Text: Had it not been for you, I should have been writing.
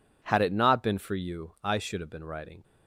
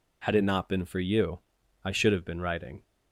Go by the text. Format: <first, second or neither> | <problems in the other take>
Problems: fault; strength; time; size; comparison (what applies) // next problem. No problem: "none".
neither | none